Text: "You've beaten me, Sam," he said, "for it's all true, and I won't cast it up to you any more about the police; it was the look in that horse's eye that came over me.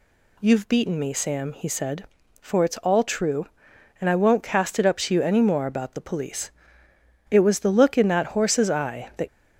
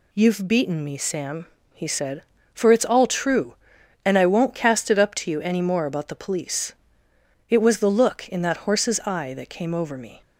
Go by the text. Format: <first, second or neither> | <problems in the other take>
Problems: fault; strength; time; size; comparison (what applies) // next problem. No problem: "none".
second | stops before "came over me"; at 9.2 s